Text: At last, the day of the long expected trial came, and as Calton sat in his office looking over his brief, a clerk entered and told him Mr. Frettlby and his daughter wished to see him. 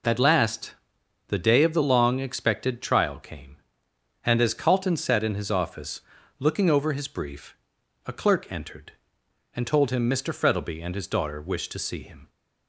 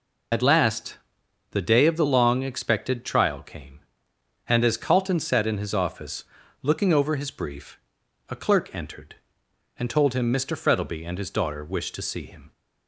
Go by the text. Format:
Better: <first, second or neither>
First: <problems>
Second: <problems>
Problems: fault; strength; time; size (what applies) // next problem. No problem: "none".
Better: first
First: pauses between "office" and "looking"; at 6.0 s; 0.38 s long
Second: loses the start of "At"; at 0.3 s; 50 ms // pauses between "office" and "looking"; at 6.2 s; 0.38 s long